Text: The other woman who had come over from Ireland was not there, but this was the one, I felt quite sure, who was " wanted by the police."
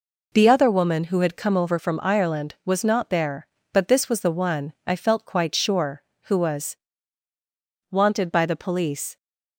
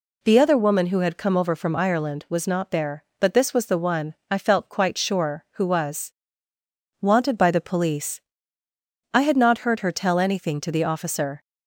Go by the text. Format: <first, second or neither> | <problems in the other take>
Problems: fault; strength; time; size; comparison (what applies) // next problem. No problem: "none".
first | goes on to say "I had not heard her tell anything to the officer"; strong; from 9.1 s on; 2.2 s long